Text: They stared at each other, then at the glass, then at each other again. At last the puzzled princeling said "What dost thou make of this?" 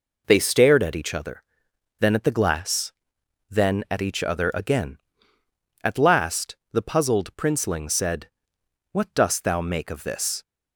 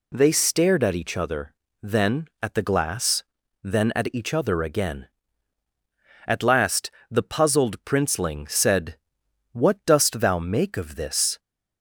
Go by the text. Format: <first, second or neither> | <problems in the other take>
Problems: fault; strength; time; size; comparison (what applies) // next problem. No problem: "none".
neither | pauses between "last" and "the"; slight; the same in both // pauses between "said" and "What"; noticeable; the same in both